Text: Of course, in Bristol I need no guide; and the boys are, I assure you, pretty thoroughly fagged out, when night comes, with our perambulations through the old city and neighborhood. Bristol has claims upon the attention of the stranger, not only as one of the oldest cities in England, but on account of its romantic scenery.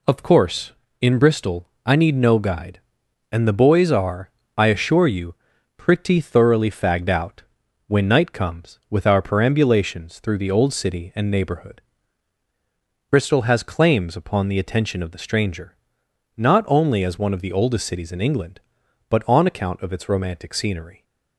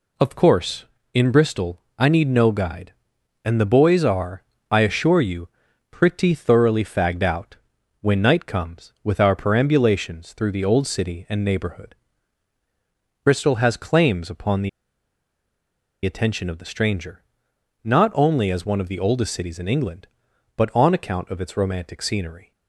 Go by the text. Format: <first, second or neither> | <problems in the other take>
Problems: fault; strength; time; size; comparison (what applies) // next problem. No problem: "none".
first | pauses between "Bristol" and "I"; slight; at 1.7 s; 0.20 s long; slight in the first // pauses between "the" and "attention"; strong; at 14.6 s; 1.3 s long